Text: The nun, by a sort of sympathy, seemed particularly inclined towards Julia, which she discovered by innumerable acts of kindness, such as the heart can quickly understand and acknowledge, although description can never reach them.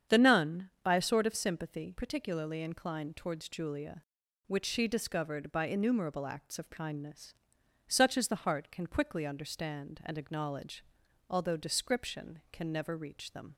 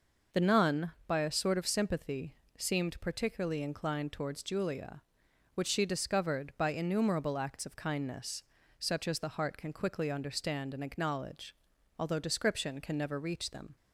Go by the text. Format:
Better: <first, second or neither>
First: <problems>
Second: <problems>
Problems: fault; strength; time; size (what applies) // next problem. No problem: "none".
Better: second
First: starts louder than the rest; strong; until 1.2 s; 8 dB // skips "seemed"; at 1.9 s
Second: none